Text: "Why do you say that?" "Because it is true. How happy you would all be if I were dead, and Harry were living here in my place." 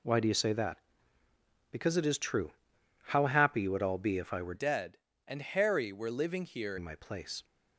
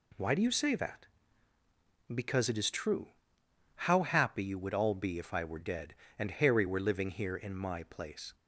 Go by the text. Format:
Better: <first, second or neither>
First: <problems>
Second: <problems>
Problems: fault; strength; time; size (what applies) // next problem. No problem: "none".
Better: second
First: changes voice from "dead" to "here"; from 4.5 to 6.7 s; 2.2 s long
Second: none